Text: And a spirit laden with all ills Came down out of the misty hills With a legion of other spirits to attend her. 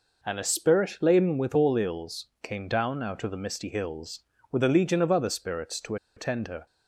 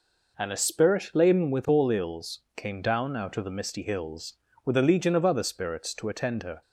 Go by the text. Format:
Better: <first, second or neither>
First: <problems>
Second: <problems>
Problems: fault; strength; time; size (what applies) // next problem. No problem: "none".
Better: second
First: pauses between "ills" and "Came"; slight; at 2.2 s; 0.16 s long // pauses between "to" and "attend"; slight; at 5.9 s; 0.21 s long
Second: pauses between "ills" and "Came"; slight; at 2.4 s; 0.16 s long